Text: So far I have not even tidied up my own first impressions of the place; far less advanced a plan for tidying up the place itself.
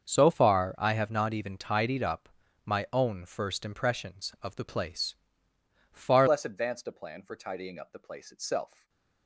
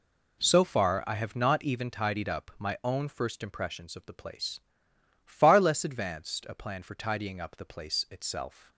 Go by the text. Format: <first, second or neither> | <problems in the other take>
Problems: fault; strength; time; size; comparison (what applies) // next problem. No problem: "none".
second | starts louder than the rest; until 1.0 s; 6.5 dB // pauses between "up" and "my"; slight; at 2.2 s; 0.36 s long // changes voice at "less"; from 6.2 s on; 2.6 s long // stays silent after the last word; slight; from 8.6 s on; 0.6 s long